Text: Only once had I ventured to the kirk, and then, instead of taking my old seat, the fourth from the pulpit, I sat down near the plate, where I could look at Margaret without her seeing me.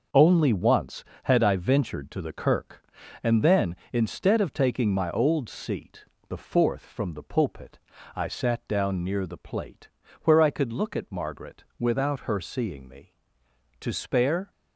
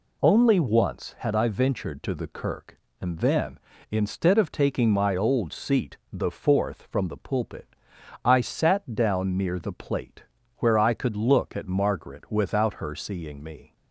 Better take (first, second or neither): second